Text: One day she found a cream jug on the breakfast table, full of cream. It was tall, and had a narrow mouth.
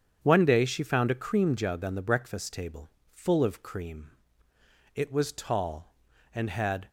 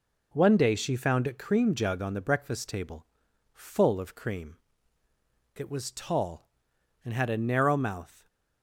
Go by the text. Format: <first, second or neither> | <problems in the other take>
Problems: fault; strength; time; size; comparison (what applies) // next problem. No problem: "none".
second | starts louder than the rest; strong; until 1.2 s; 8 dB // stops before "a narrow mouth"; at 6.8 s